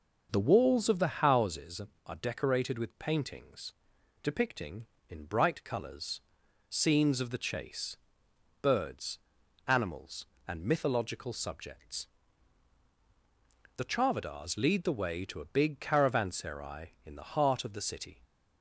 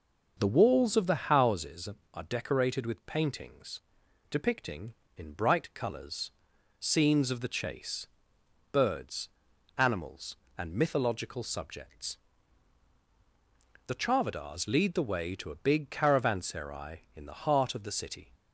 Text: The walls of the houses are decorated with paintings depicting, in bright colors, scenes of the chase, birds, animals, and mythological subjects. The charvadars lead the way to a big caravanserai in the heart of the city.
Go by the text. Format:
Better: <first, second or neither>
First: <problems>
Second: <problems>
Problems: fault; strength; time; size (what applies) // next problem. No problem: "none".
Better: neither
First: pauses between "paintings" and "depicting"; noticeable; at 3.7 s; 0.50 s long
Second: pauses between "paintings" and "depicting"; noticeable; at 3.7 s; 0.50 s long